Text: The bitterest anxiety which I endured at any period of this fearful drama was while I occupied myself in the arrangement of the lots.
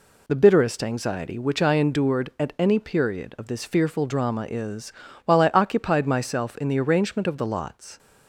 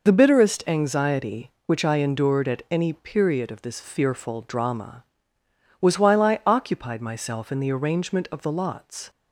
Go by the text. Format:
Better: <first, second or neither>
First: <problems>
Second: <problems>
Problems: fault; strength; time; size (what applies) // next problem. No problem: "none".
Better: second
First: says "is" for "was"; at 4.4 s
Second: none